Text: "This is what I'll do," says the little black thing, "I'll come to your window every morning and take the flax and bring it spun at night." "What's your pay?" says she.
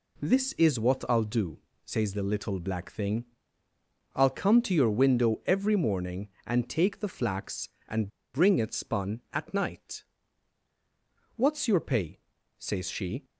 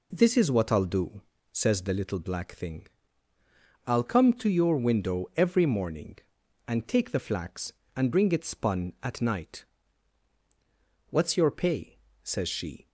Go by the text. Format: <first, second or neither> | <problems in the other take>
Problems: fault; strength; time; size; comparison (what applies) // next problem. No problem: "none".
second | pauses between "and" and "bring"; slight; at 8.0 s; 0.25 s long